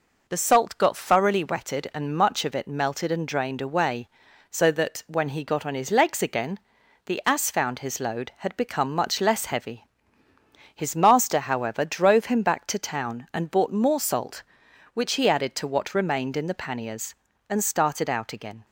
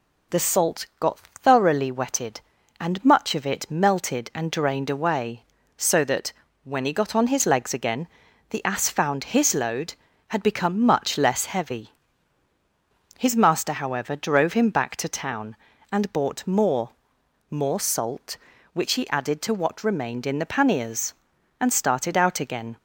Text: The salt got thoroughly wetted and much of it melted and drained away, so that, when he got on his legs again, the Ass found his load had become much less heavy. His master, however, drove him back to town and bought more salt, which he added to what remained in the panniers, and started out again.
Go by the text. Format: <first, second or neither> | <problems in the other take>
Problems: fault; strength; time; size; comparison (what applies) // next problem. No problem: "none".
first | says "more" twice; at 17.5 s